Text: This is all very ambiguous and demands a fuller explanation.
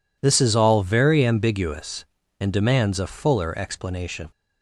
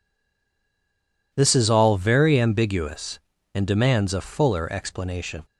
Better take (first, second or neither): first